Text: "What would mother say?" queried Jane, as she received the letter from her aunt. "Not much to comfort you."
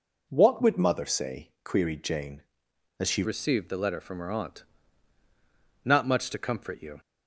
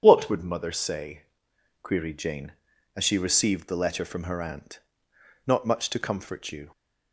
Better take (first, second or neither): second